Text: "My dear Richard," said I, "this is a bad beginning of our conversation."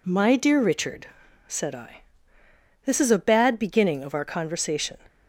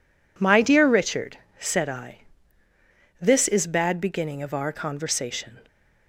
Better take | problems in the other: first | skips "a"; at 3.6 s

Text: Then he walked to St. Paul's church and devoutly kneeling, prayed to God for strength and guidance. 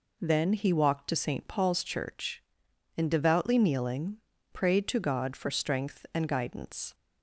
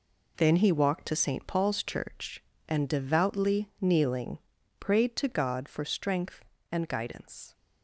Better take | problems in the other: first | gets quieter; strong; throughout; 9 dB

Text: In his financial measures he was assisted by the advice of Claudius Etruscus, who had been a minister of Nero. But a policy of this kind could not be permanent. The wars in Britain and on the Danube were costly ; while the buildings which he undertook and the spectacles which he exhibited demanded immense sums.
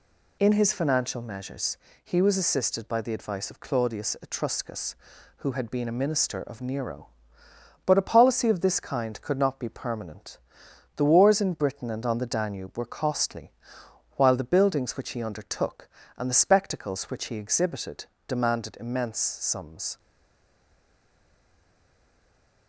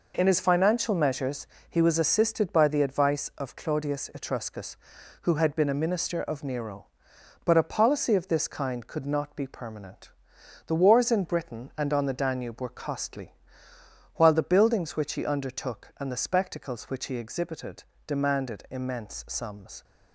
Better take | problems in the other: second | pauses between "measures" and "he"; slight; at 1.7 s; 0.26 s long; slight in the second // pauses between "exhibited" and "demanded"; slight; at 18.0 s; 0.20 s long; slight in the second // stays silent after the last word; strong; from 19.9 s on; 2.7 s long

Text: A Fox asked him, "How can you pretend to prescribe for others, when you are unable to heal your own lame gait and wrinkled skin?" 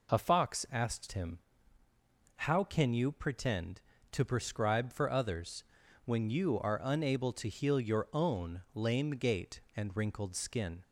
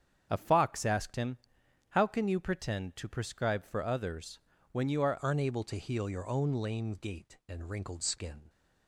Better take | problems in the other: first | starts louder than the rest; strong; until 1.3 s; 7.5 dB // changes voice at "unable"; from 5.2 s on; 3.2 s long

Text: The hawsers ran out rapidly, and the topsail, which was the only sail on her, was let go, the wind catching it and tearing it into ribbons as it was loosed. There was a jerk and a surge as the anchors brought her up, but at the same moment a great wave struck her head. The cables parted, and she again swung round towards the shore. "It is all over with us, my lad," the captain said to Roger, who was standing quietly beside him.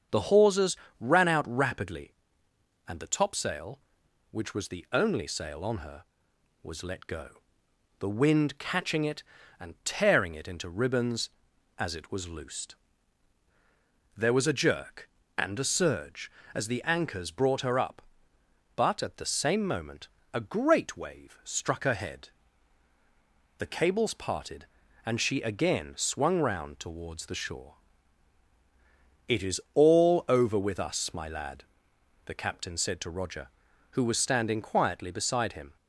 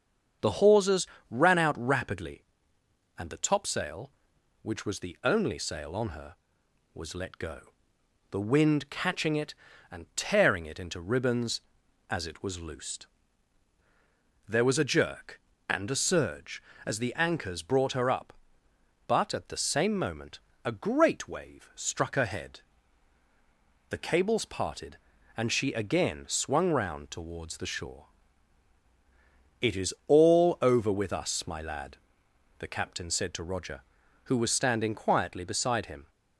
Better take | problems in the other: neither | starts louder than the rest; strong; the same in both // pauses between "hawsers" and "ran"; slight; the same in both // pauses between "moment" and "a"; slight; the same in both

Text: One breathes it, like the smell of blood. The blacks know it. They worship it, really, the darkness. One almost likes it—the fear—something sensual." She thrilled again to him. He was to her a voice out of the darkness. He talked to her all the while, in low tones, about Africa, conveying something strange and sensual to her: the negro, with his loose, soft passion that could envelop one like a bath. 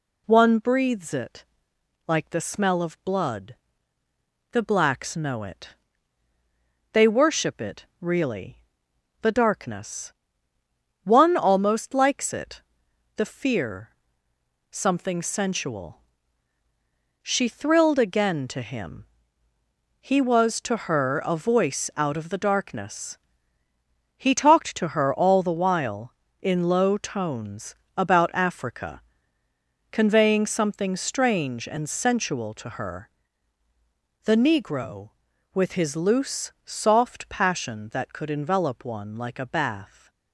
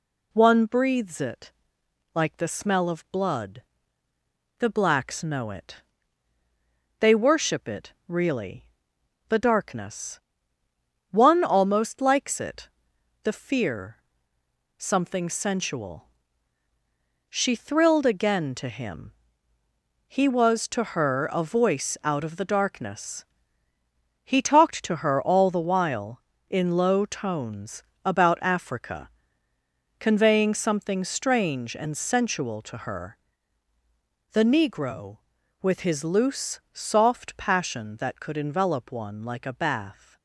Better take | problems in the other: neither | none

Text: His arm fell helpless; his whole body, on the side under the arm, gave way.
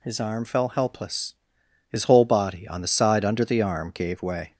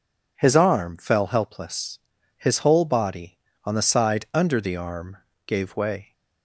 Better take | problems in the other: neither | none

